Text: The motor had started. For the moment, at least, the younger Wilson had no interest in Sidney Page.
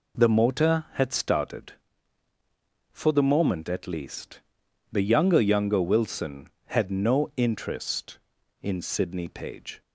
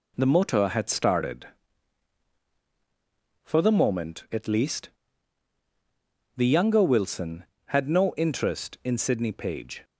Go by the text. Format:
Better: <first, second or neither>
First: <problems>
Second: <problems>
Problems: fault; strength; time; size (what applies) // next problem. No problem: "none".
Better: second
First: says "younger" twice; at 5.4 s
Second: none